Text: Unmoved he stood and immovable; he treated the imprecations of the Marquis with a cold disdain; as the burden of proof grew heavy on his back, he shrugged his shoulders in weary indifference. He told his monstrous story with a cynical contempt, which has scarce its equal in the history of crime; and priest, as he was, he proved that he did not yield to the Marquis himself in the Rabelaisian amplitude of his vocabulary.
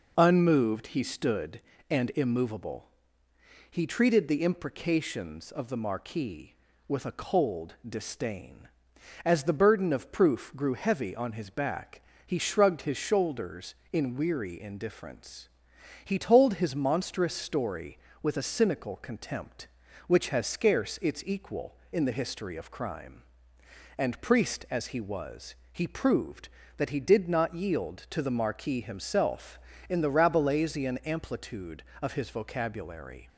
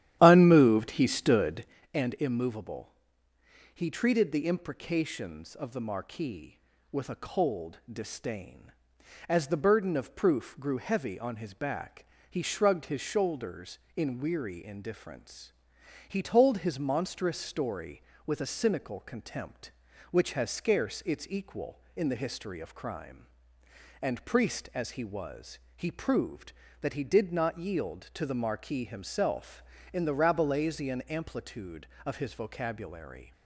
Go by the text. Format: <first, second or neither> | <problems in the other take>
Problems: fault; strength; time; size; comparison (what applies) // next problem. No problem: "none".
first | starts louder than the rest; strong; until 1.8 s; 11.5 dB